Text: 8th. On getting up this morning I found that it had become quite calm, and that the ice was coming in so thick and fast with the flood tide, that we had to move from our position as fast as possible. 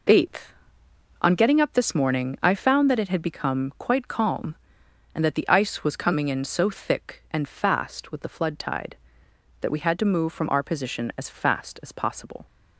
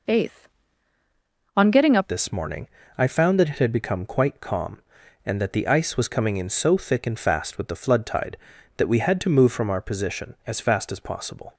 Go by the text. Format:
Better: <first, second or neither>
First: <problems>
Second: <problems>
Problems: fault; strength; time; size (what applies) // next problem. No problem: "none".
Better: first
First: none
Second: changes voice at "this"; from 2.0 s on; 9.5 s long // pauses between "morning" and "I"; slight; at 2.6 s; 0.32 s long